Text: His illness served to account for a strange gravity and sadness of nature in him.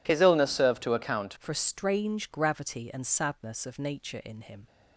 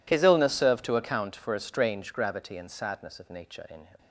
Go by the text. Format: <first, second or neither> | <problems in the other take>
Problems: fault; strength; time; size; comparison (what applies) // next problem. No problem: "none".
second | changes voice at "for"; from 1.3 s on; 3.3 s long